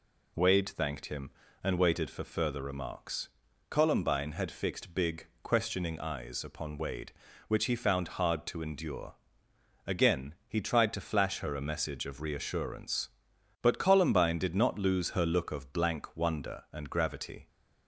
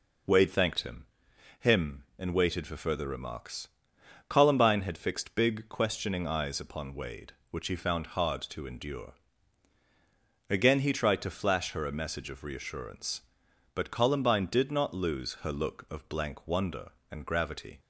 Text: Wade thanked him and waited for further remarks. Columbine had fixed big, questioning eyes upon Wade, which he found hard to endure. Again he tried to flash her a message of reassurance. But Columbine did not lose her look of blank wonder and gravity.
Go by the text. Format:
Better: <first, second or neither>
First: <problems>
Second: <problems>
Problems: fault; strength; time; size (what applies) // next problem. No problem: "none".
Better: first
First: none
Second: says "him" twice; at 1.5 s